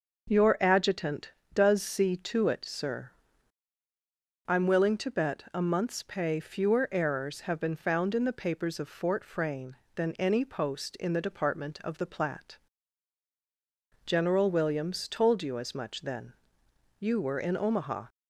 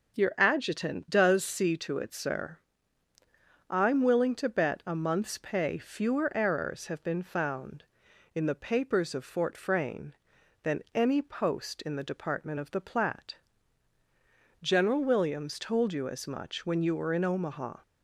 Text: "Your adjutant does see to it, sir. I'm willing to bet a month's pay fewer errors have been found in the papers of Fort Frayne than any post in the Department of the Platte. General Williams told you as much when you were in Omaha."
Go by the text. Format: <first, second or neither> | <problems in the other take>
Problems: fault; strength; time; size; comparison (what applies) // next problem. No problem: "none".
second | starts louder than the rest; noticeable; until 1.5 s; 6 dB // says "then" for "when"; at 16.0 s